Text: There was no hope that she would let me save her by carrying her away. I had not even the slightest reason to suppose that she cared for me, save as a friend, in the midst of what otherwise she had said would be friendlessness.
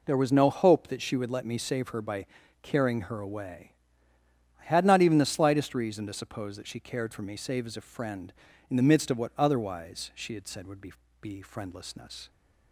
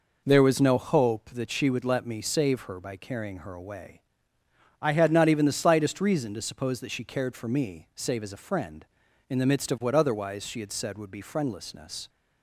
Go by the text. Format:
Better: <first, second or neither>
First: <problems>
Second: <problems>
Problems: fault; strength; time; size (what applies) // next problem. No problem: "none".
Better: second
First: pauses between "by" and "carrying"; slight; at 2.2 s; 0.36 s long // says "be" twice; at 11.1 s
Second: none